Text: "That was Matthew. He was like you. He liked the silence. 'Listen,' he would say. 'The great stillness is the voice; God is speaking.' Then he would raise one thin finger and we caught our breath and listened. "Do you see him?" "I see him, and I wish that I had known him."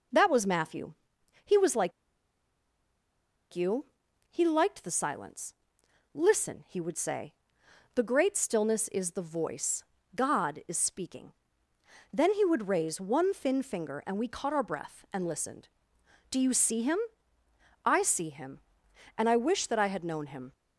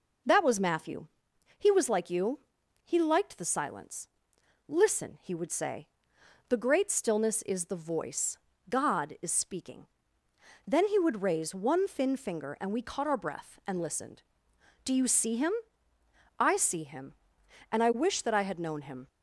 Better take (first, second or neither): second